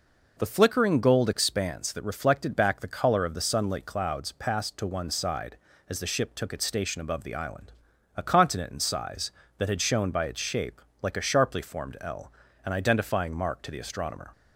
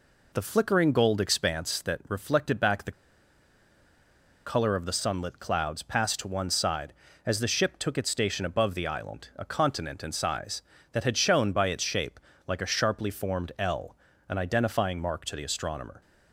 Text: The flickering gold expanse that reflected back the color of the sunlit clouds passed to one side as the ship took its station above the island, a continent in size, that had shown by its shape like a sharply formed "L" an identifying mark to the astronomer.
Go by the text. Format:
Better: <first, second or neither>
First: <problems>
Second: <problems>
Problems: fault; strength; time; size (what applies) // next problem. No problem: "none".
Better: first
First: pauses between "shape" and "like"; slight; at 10.8 s; 0.20 s long // pauses between "L" and "an"; slight; at 12.3 s; 0.34 s long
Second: pauses between "the" and "color"; strong; at 2.9 s; 1.5 s long // pauses between "shape" and "like"; slight; at 12.1 s; 0.28 s long // pauses between "L" and "an"; slight; at 13.9 s; 0.36 s long